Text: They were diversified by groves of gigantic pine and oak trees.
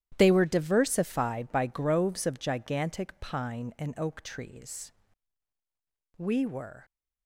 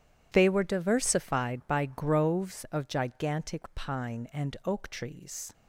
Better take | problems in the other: second | starts louder than the rest; strong; until 1.1 s; 11.5 dB // goes on to say "We were"; noticeable; from 6.1 s on; 0.68 s long

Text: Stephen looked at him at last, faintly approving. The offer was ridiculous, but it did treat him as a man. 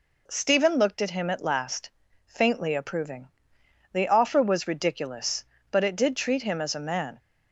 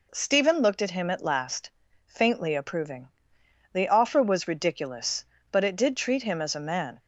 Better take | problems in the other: neither | none

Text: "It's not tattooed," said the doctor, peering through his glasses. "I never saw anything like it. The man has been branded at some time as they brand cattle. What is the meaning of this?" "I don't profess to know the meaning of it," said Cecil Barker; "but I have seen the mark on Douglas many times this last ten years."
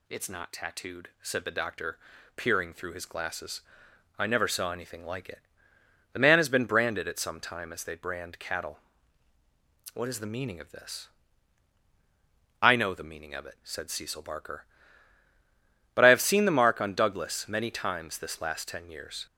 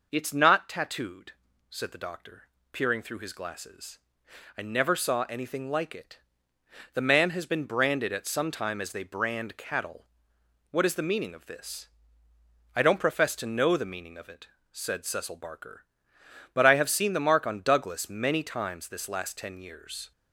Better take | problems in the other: second | skips "don't profess to"; at 12.7 s

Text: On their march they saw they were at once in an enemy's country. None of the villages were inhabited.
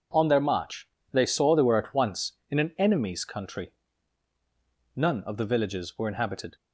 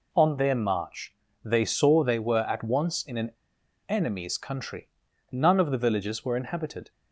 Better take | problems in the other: first | pauses between "march" and "they"; slight; at 1.1 s; 0.28 s long; slight in the first // pauses between "an" and "enemy's"; noticeable; at 3.3 s; 0.57 s long

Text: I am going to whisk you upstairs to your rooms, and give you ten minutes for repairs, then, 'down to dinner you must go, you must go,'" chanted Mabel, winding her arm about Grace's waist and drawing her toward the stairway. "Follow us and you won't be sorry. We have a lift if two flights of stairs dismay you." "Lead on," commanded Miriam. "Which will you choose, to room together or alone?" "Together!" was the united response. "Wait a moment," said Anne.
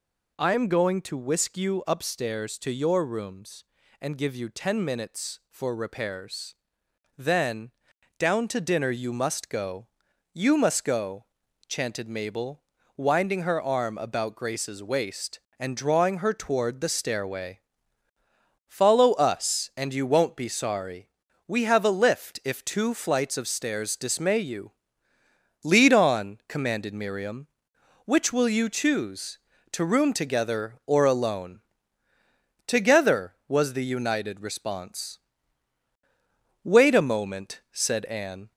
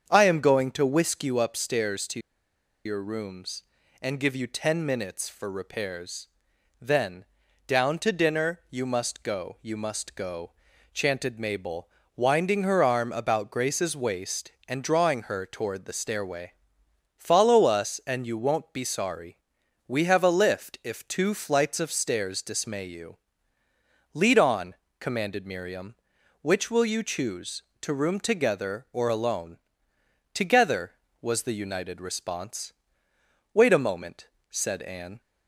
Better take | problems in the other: first | starts louder than the rest; strong; until 1.1 s; 7.5 dB // pauses between "to" and "your"; noticeable; at 2.1 s; 0.65 s long

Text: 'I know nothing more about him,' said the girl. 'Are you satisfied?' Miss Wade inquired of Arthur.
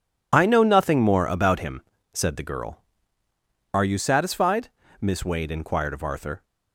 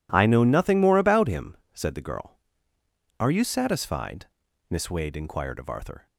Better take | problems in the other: second | loses the start of "I"; at 0.3 s; 40 ms

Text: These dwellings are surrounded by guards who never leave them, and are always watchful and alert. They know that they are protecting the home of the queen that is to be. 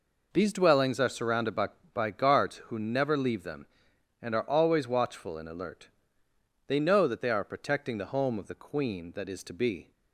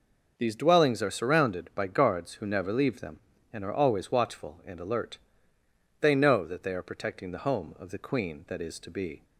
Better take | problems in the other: second | says "by" twice; at 1.9 s

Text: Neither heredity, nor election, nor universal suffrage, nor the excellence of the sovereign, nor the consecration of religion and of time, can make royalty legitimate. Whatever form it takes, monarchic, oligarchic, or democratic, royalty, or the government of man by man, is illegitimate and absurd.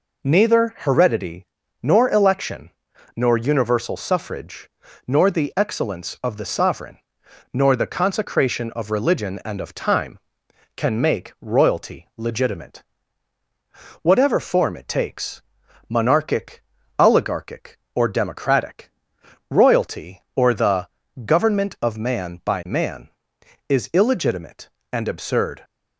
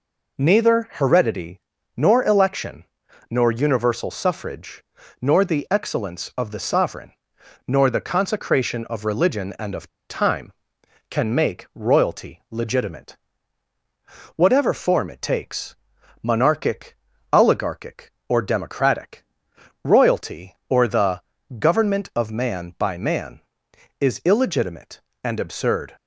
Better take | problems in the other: first | pauses between "of" and "time"; slight; at 9.8 s; 0.21 s long // pauses between "the" and "government"; slight; at 21.2 s; 0.36 s long; slight in the first

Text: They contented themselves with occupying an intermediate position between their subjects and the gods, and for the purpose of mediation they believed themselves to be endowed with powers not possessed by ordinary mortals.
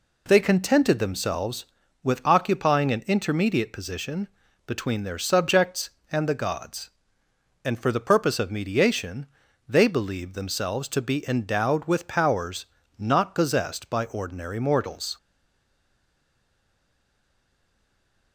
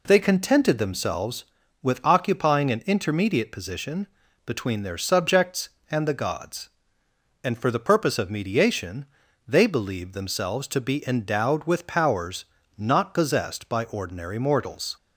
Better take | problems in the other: second | pauses between "position" and "between"; at 4.2 s; 0.40 s long; also in the second // pauses between "mediation" and "they"; at 9.2 s; 0.42 s long; also in the second // pauses between "powers" and "not"; slight; at 12.6 s; 0.34 s long; slight in the second // stays silent after the last word; strong; from 15.1 s on; 3.2 s long

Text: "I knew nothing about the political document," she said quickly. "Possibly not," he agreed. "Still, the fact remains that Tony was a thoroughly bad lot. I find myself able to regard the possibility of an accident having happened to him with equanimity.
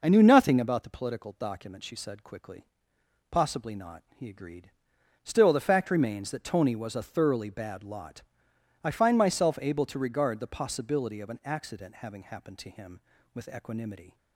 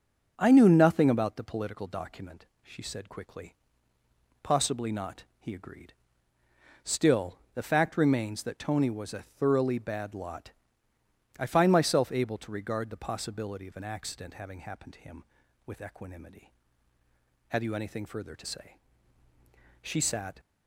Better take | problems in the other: first | starts louder than the rest; until 1.3 s; 7 dB // goes on to say "Have you anything further to say She sat"; strong; from 17.4 s on; 2.9 s long

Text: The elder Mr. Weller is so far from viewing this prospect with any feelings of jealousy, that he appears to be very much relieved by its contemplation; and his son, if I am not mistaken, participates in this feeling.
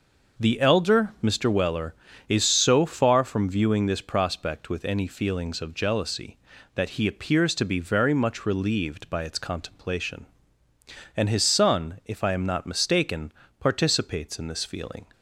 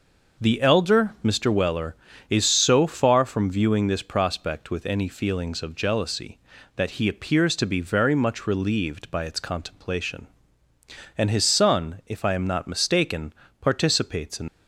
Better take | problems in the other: first | stops before "this feeling"; at 14.4 s

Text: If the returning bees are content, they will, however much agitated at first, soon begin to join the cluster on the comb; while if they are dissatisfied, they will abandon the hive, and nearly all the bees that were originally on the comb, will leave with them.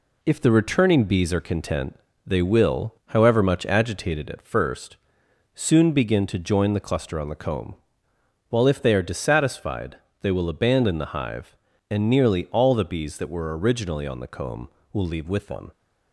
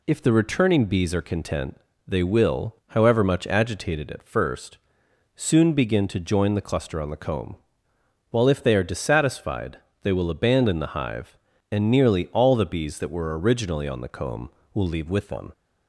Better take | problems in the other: second | gets quieter; noticeable; throughout; 4 dB

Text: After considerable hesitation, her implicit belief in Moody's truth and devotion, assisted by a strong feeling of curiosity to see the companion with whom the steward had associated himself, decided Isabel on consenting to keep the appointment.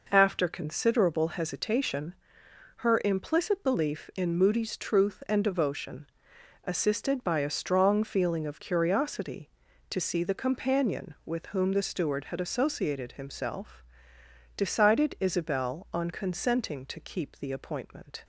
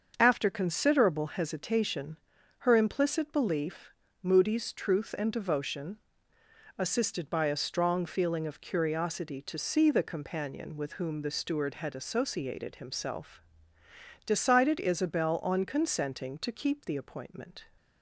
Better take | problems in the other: first | starts louder than the rest; until 1.1 s; 7 dB // skips "in"; at 4.0 s

